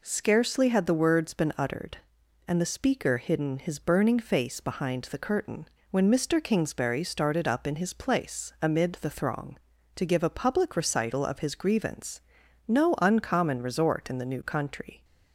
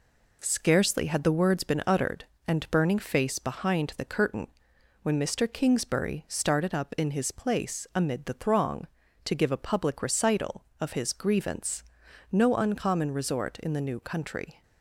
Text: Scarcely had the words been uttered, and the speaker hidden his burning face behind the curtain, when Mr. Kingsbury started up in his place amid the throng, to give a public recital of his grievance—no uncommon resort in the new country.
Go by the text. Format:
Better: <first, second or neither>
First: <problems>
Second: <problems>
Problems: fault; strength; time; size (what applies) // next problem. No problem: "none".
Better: first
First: none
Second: skips "the speaker hidden his"; at 2.7 s